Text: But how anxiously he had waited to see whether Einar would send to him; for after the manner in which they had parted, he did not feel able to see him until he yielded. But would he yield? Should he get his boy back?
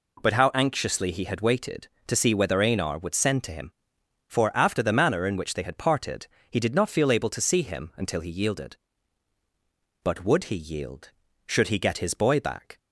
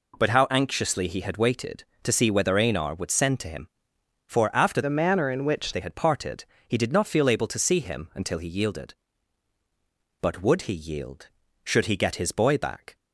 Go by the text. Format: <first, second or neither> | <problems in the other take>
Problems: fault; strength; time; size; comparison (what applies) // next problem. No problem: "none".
first | changes voice from "the" to "which"; from 4.8 to 5.7 s; 0.9 s long